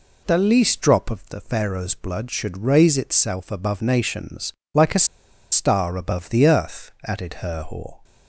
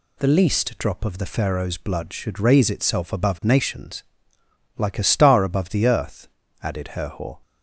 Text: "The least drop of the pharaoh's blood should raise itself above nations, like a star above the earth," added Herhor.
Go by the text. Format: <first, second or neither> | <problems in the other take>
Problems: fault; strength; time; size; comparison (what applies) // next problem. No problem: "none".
second | pauses between "a" and "star"; noticeable; at 5.0 s; 0.46 s long